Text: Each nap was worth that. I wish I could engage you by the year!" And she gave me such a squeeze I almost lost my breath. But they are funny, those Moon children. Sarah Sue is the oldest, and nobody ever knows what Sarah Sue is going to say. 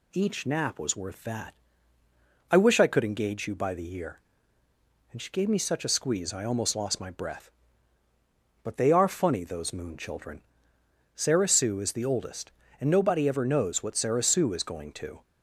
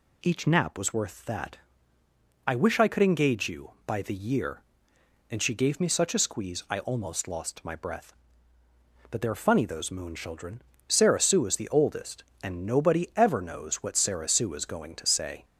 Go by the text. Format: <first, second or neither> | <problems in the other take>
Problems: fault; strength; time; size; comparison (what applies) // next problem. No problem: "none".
second | stops before "say"; at 15.2 s